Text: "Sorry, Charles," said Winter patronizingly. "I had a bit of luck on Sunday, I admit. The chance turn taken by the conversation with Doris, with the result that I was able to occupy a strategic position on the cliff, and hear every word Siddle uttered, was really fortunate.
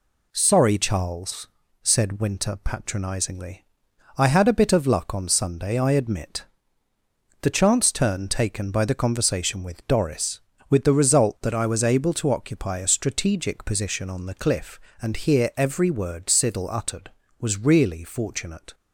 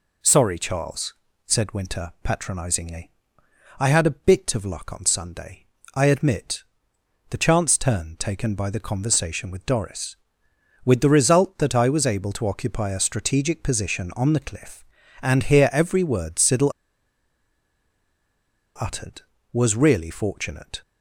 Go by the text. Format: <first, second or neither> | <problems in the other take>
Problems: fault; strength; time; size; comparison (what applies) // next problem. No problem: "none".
first | pauses between "Siddle" and "uttered"; strong; at 16.7 s; 2.0 s long